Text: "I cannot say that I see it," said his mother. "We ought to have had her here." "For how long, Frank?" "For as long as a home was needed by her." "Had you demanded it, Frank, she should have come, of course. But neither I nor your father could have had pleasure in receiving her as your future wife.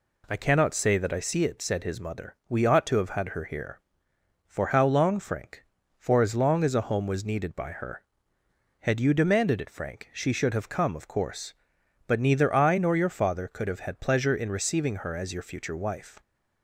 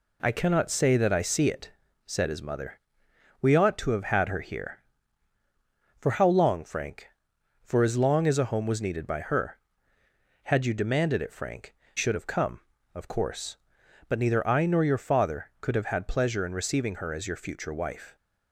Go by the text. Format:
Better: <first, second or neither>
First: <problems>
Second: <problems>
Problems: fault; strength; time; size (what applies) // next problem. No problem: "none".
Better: first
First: none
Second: skips "she"; at 11.8 s